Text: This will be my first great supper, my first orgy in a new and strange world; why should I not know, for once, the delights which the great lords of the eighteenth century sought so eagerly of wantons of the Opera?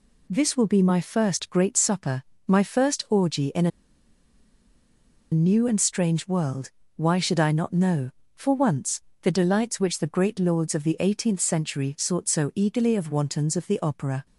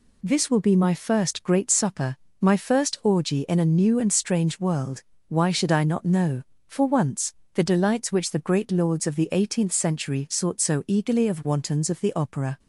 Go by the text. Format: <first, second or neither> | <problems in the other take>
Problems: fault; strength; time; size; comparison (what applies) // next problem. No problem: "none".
second | pauses between "a" and "new"; strong; at 3.7 s; 1.6 s long